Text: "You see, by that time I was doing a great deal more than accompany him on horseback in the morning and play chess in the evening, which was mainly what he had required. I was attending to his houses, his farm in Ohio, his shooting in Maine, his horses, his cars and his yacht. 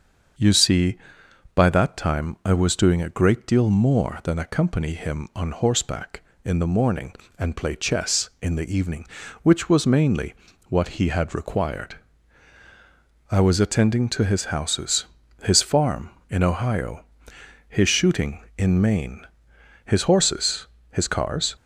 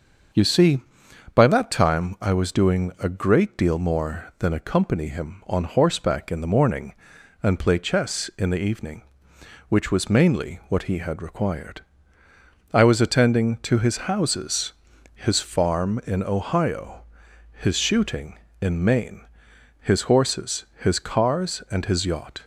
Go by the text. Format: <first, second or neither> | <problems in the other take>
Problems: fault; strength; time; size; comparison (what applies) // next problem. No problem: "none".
second | starts louder than the rest; until 1.9 s; 6.5 dB; also in the second // pauses between "mainly" and "what"; slight; at 10.3 s; 0.34 s long // stops before "and his yacht"; at 21.5 s